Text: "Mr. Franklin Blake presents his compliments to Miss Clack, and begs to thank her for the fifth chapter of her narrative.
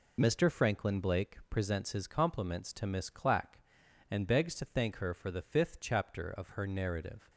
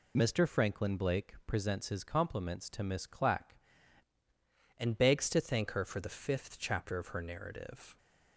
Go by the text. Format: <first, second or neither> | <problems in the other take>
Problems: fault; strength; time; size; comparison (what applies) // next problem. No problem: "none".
first | changes voice at "and"; from 4.7 s on; 3.2 s long